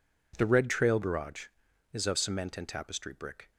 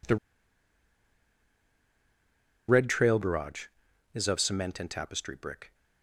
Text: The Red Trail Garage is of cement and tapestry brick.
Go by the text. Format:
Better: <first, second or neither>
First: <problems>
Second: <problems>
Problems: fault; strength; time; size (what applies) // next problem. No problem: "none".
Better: first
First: none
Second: pauses between "The" and "Red"; strong; at 0.1 s; 2.5 s long